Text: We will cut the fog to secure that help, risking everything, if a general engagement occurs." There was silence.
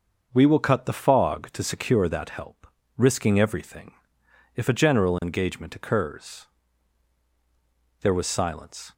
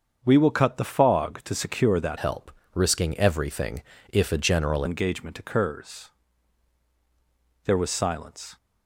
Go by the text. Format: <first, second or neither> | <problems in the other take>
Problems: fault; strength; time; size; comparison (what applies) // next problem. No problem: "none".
first | starts louder than the rest; until 1.2 s; 6.5 dB; also in the first // changes voice from "help" to "general"; from 2.1 to 4.8 s; 2.7 s long